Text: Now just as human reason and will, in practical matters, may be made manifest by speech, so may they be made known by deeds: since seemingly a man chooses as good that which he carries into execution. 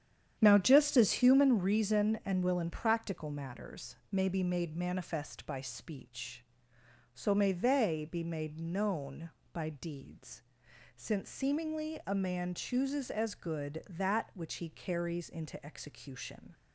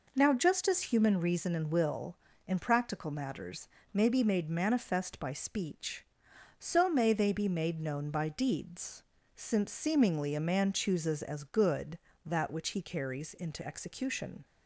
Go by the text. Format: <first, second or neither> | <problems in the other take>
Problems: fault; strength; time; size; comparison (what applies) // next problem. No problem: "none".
second | starts louder than the rest; strong; until 1.3 s; 9 dB